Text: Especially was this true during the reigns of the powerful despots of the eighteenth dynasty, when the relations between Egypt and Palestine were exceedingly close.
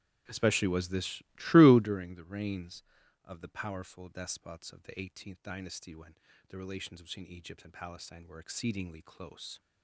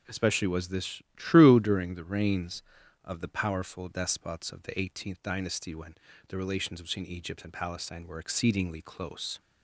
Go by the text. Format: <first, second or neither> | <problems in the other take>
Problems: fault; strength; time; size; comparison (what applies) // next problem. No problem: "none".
second | starts louder than the rest; strong; until 1.9 s; 11.5 dB // pauses between "when" and "the"; slight; at 6.1 s; 0.32 s long; slight in the second